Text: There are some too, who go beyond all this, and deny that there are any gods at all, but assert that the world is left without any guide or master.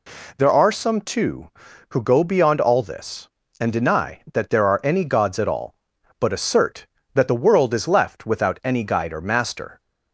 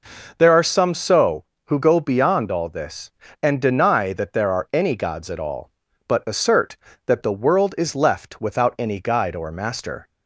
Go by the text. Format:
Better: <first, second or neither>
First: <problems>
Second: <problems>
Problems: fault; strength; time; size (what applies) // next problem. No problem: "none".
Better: first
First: none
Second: says "so" for "too"; at 0.9 s